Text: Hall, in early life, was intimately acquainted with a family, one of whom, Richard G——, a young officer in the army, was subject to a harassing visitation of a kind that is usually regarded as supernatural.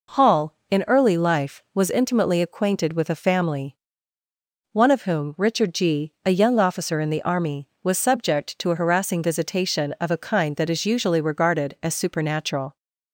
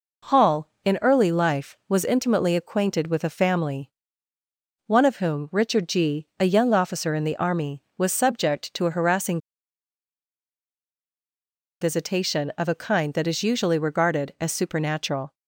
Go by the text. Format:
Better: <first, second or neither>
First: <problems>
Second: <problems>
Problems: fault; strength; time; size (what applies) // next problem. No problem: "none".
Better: first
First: none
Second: pauses between "harassing" and "visitation"; strong; at 9.3 s; 2.4 s long